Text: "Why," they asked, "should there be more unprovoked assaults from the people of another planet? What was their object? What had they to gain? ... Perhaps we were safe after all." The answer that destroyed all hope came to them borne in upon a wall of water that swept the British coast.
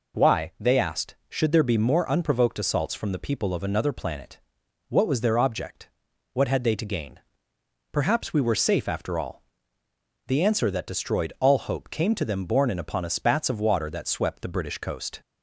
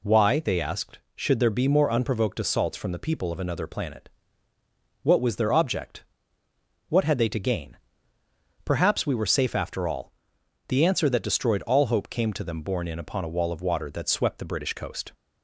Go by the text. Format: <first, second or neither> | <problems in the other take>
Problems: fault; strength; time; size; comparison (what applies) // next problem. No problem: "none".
second | says "spats" for "wall"; at 13.0 s